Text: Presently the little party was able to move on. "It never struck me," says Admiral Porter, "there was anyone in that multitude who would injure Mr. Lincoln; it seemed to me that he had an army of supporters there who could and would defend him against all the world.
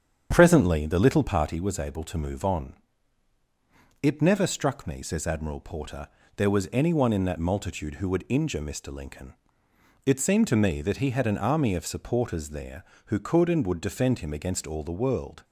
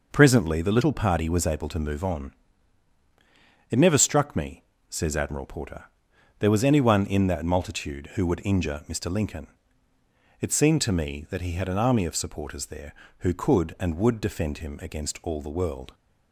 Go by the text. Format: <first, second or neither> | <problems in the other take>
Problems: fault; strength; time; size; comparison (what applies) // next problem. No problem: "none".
second | starts louder than the rest; strong; until 1.4 s; 8 dB